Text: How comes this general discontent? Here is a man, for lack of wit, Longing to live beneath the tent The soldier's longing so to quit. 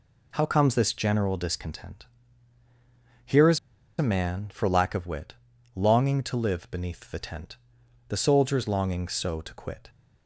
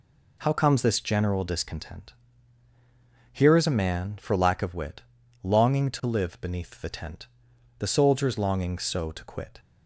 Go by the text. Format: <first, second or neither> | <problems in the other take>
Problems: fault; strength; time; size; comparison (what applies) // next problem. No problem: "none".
second | pauses between "is" and "a"; at 3.5 s; 0.40 s long // pauses between "tent" and "The"; noticeable; at 7.5 s; 0.54 s long; noticeable in the second